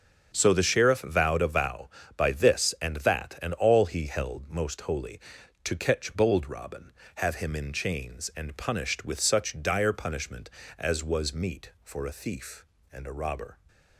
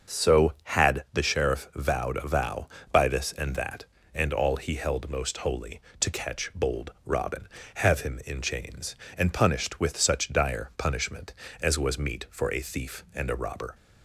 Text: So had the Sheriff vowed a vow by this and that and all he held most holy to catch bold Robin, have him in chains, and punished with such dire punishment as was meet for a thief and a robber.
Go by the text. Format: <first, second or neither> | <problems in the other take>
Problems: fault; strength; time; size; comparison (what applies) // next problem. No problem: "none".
second | starts louder than the rest; until 1.3 s; 7 dB; also in the second // skips "had"; at 0.5 s